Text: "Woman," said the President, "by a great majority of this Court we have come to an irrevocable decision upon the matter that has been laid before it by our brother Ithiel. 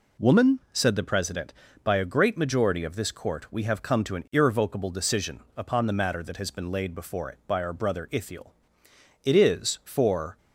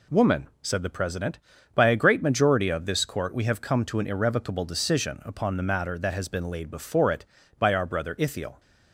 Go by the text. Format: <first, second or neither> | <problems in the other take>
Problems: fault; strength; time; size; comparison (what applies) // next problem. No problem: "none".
second | pauses between "decision" and "upon"; slight; at 5.3 s; 0.18 s long // goes on to say "It is for"; noticeable; from 9.2 s on; 1.1 s long